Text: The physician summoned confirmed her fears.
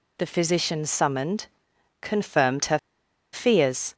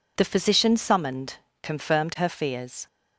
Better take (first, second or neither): second